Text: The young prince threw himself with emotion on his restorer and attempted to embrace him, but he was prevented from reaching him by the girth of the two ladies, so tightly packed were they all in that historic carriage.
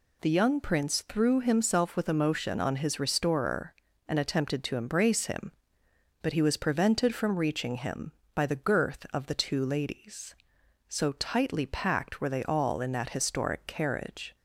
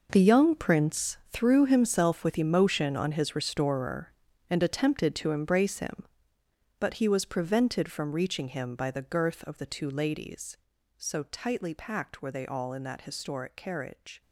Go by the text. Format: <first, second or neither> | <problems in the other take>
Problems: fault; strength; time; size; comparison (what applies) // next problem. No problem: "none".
first | gets quieter; strong; throughout; 14 dB